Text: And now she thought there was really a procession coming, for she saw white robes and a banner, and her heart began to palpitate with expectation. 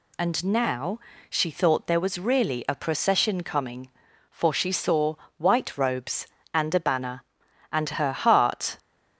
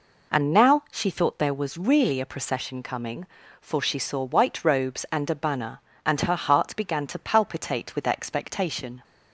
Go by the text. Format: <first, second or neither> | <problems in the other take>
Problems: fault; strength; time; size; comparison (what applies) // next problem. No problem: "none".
second | pauses between "now" and "she"; slight; at 1.0 s; 0.28 s long // pauses between "saw" and "white"; slight; at 5.1 s; 0.24 s long // stops before "began to palpitate with expectation"; at 8.7 s